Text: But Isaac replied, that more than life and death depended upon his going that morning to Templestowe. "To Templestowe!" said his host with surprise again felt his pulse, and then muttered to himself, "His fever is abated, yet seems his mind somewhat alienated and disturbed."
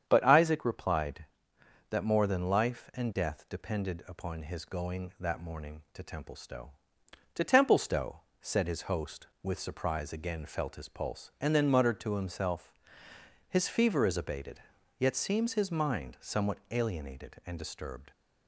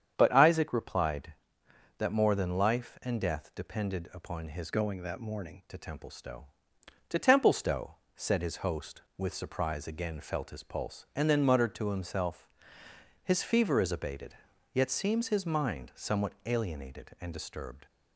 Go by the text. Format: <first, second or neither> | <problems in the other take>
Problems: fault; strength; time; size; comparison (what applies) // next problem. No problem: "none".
first | starts louder than the rest; strong; until 1.1 s; 8 dB; strong in the first // changes voice from "going" to "morning"; from 4.6 to 5.6 s; 1.0 s long